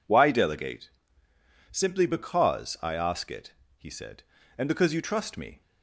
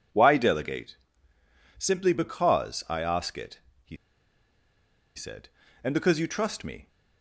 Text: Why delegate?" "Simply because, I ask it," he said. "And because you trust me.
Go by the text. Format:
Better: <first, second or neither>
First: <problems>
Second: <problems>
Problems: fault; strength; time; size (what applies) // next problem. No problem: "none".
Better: first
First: none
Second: pauses between "he" and "said"; at 3.9 s; 1.1 s long